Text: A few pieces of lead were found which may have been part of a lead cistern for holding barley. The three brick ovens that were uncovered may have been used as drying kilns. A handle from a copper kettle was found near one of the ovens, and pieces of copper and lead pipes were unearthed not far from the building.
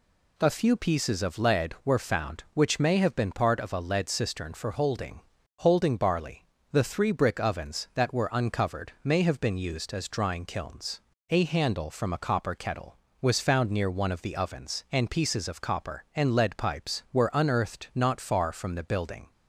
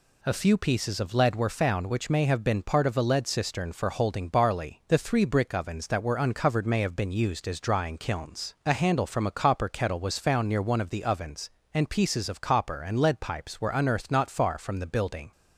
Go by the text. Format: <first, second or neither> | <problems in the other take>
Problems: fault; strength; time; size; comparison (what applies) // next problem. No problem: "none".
second | says "holding" twice; at 5.6 s